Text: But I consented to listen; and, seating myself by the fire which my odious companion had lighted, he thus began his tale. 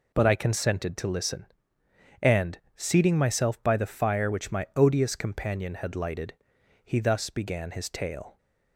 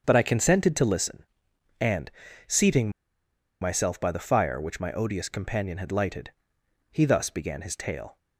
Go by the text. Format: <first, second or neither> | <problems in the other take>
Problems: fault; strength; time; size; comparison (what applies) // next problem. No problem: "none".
first | starts louder than the rest; until 1.0 s; 7 dB // pauses between "seating" and "myself"; noticeable; at 2.8 s; 0.71 s long